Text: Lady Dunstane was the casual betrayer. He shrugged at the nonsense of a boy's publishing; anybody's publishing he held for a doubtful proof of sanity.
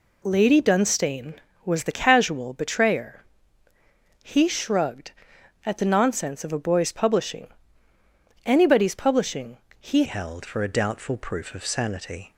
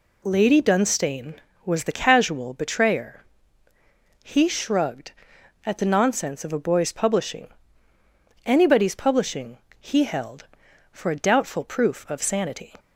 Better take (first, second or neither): second